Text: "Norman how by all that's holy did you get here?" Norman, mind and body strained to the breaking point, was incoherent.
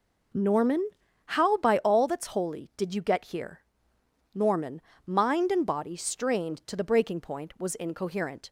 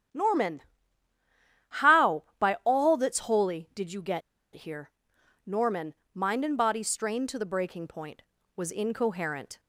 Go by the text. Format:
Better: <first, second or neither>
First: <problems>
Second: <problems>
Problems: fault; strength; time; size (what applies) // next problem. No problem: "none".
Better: first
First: pauses between "Norman" and "how"; at 0.8 s; 0.38 s long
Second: starts louder than the rest; strong; until 2.2 s; 9.5 dB // pauses between "Norman" and "how"; at 0.6 s; 1.1 s long // pauses between "get" and "here"; slight; at 4.2 s; 0.34 s long